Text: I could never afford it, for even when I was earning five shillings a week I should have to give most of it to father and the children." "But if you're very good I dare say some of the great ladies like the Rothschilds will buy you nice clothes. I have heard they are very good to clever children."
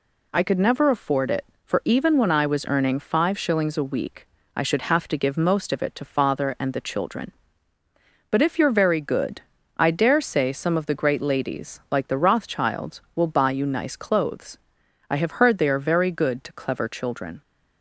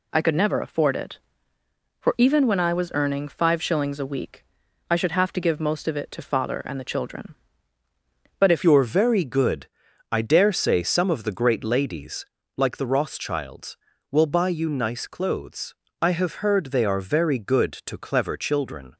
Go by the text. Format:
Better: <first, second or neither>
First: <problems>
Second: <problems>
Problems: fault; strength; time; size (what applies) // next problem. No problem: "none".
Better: first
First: pauses between "week" and "I"; slight; at 4.2 s; 0.28 s long // pauses between "good" and "I"; slight; at 9.4 s; 0.36 s long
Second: pauses between "week" and "I"; at 4.4 s; 0.44 s long // changes voice at "you're"; from 8.6 s on; 10.3 s long // pauses between "good" and "I"; at 9.6 s; 0.44 s long // pauses between "ladies" and "like"; slight; at 12.2 s; 0.32 s long